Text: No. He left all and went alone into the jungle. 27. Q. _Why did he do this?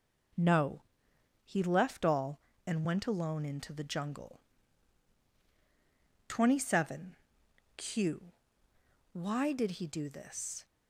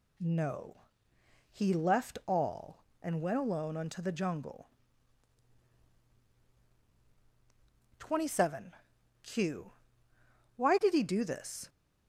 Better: first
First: none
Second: says "unto" for "into"; at 3.7 s

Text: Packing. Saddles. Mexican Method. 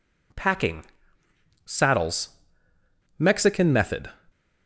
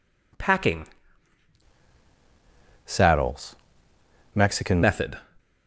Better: first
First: none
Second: changes voice from "Saddles" to "Mexican"; from 2.8 to 4.8 s; 2.0 s long

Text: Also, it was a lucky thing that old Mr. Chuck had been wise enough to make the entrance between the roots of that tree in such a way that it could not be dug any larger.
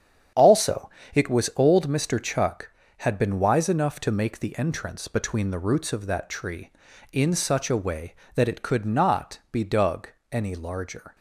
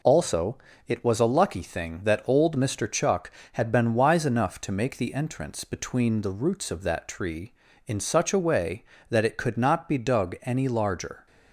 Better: second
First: starts louder than the rest; strong; until 1.6 s; 9 dB // skips "a lucky thing that"; at 1.5 s // pauses between "dug" and "any"; slight; at 10.0 s; 0.22 s long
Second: none

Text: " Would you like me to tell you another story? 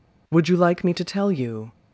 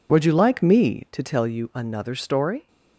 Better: second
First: stops before "another story"; at 1.7 s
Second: none

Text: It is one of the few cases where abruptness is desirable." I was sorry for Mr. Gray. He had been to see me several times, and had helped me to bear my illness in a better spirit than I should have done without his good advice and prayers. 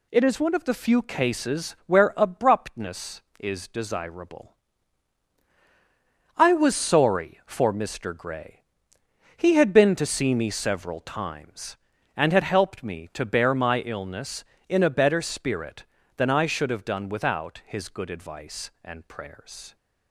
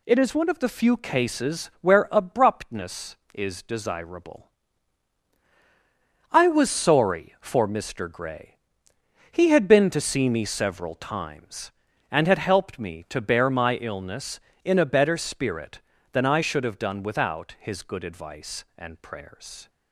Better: neither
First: none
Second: none

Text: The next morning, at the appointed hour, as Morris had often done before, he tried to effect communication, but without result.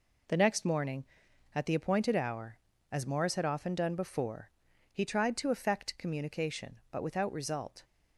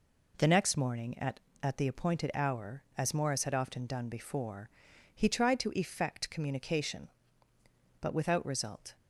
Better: first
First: none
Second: says "at" twice; at 1.6 s

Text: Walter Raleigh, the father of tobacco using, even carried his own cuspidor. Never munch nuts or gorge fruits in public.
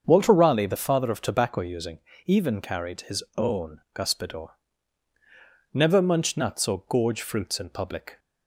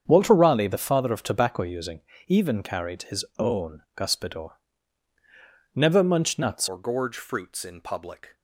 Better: first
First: starts louder than the rest; until 1.0 s; 6.5 dB // pauses between "own" and "cuspidor"; slight; at 3.7 s; 0.16 s long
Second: starts louder than the rest; strong; until 1.0 s; 7.5 dB // pauses between "own" and "cuspidor"; slight; at 3.8 s; 0.16 s long // changes voice at "or"; from 6.6 s on; 1.7 s long

